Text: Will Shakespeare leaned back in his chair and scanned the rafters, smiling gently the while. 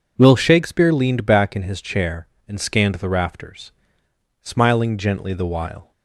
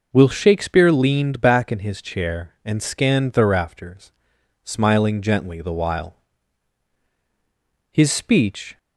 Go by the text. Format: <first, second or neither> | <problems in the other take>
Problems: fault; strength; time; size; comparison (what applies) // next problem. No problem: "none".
first | goes on to say "His speech"; noticeable; from 7.9 s on; 0.86 s long